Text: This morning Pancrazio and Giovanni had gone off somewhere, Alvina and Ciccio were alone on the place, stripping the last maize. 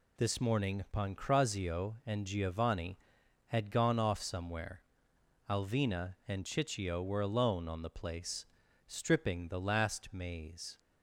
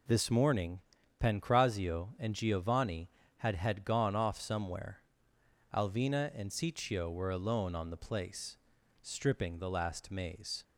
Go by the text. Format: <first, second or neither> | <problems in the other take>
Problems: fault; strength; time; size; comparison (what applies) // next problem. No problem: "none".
first | pauses between "morning" and "Pancrazio"; at 0.7 s; 0.42 s long // says "had" twice; at 3.5 s